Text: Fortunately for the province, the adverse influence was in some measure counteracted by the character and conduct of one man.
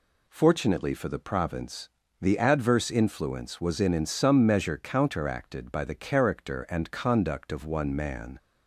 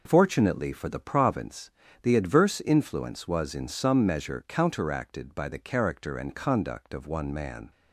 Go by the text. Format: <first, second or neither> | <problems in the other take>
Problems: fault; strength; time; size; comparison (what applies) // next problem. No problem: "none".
second | says "in" twice; at 3.9 s